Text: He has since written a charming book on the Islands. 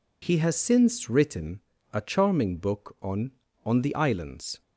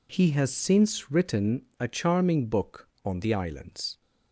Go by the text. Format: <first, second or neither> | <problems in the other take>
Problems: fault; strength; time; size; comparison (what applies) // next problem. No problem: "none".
second | pauses between "written" and "a"; slight; at 1.5 s; 0.32 s long; slight in the second // says "on" twice; at 3.6 s